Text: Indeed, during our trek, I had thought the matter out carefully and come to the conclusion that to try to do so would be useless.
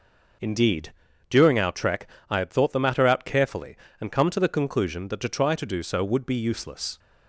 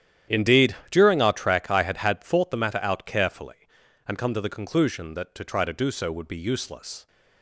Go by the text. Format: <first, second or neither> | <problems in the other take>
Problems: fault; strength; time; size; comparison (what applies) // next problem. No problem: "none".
first | starts louder than the rest; strong; until 1.4 s; 10.5 dB // says "had" twice; at 1.9 s